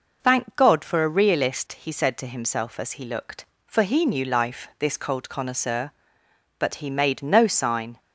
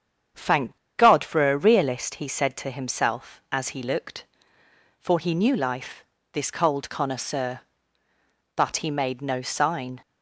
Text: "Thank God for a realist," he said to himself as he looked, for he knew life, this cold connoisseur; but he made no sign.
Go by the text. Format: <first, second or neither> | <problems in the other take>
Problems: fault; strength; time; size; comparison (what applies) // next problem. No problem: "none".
first | starts louder than the rest; strong; until 1.5 s; 8 dB // pauses between "Thank" and "God"; slight; at 0.7 s; 0.21 s long